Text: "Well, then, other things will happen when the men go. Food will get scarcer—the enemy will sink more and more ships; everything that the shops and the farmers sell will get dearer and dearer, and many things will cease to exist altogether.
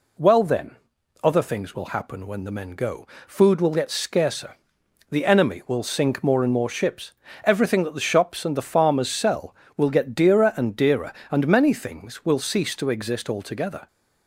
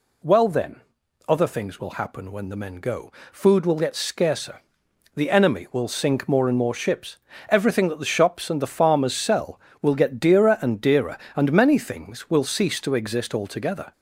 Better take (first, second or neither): first